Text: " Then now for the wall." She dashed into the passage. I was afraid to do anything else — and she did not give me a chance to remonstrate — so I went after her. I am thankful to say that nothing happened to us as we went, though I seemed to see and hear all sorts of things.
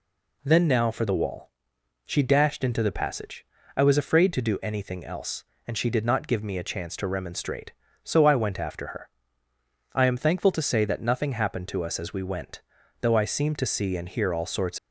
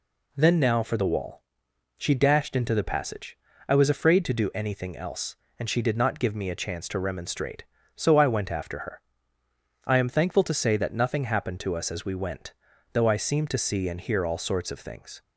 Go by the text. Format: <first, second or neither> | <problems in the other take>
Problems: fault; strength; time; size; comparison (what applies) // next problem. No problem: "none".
second | stops before "of things"; at 14.7 s